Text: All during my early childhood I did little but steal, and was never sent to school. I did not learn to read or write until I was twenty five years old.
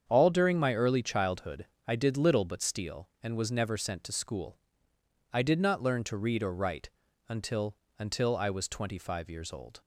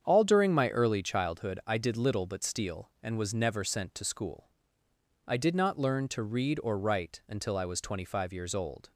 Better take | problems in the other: second | starts louder than the rest; strong; until 1.0 s; 7.5 dB; strong in the second // pauses between "childhood" and "I"; slight; at 1.6 s; 0.22 s long // pauses between "write" and "until"; at 6.9 s; 0.38 s long // says "until" twice; at 7.9 s

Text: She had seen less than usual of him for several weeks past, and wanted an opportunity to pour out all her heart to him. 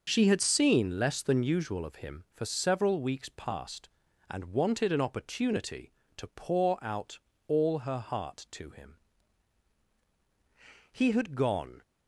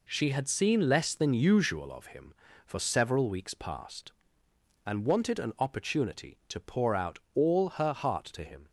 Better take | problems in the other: second | pauses between "out" and "all"; slight; at 7.1 s; 0.28 s long // goes on to say "He had gone"; noticeable; from 10.9 s on; 0.88 s long

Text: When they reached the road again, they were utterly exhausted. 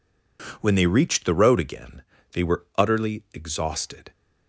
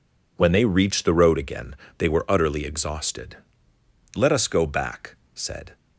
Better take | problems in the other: first | goes on to say "Let us go back said"; from 4.1 s on; 1.6 s long

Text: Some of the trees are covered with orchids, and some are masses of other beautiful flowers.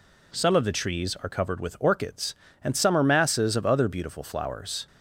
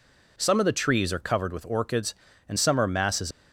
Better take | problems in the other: first | stops before "of other beautiful flowers"; at 3.3 s

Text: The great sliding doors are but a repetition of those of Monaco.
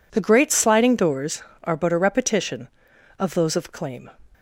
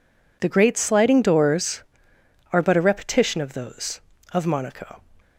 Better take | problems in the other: second | says "Claim" for "Monaco"; at 3.7 s

